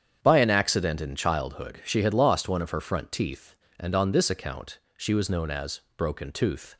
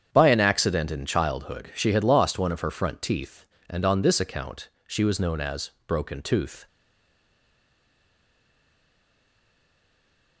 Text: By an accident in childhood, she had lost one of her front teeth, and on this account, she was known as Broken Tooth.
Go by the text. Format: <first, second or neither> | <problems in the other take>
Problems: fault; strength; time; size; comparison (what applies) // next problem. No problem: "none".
first | starts louder than the rest; strong; until 1.1 s; 8.5 dB; strong in the first // pauses between "as" and "Broken"; slight; at 5.7 s; 0.16 s long; slight in the first // stays silent after the last word; strong; from 6.6 s on; 3.8 s long